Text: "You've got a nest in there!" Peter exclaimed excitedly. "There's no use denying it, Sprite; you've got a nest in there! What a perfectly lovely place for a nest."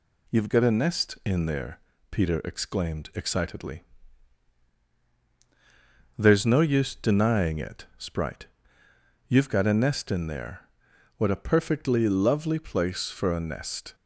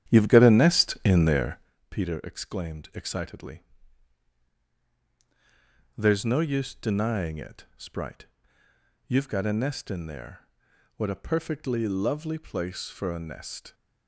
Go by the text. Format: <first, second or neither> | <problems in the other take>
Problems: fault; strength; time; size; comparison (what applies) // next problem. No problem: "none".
first | starts louder than the rest; strong; until 1.8 s; 10 dB